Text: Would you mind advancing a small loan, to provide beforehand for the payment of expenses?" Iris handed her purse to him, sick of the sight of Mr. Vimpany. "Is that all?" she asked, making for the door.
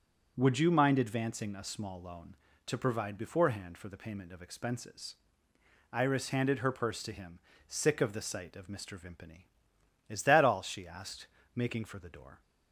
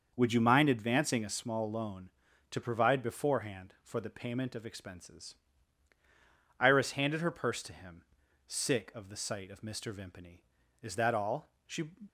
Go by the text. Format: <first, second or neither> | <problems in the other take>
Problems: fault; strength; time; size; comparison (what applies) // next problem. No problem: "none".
first | starts louder than the rest; until 1.1 s; 6.5 dB // stops before "asked making for the door"; at 12.0 s